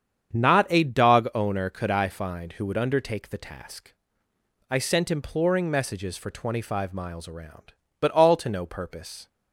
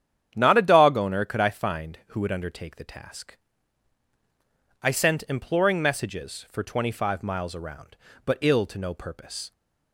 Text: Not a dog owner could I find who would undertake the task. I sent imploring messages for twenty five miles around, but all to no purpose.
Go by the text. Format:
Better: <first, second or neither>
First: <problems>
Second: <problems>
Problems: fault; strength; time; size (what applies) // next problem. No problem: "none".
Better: first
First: starts louder than the rest; strong; until 1.4 s; 8 dB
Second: starts louder than the rest; strong; until 1.3 s; 9 dB // says "ill" for "all"; at 8.4 s